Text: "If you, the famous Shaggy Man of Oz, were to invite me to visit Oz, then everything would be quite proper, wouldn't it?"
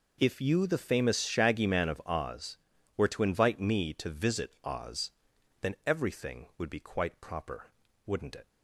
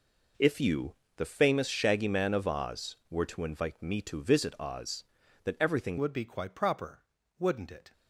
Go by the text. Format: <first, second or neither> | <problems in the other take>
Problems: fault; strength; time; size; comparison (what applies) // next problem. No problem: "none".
first | changes voice at "would"; from 5.9 s on; 2.0 s long